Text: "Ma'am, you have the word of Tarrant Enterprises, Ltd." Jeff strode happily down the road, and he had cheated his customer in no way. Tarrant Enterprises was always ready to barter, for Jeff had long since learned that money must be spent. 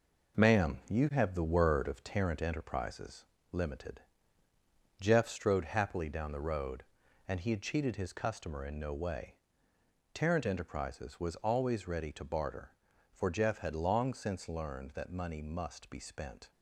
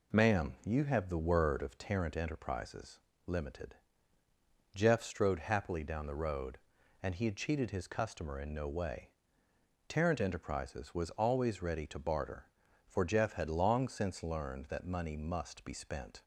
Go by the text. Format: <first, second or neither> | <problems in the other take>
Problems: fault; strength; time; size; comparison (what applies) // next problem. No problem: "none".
second | gets quieter; strong; throughout; 7.5 dB